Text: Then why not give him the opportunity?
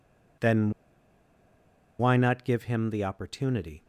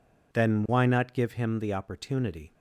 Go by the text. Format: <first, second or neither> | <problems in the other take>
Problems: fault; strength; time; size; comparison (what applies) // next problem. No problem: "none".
second | pauses between "Then" and "why"; strong; at 0.6 s; 1.2 s long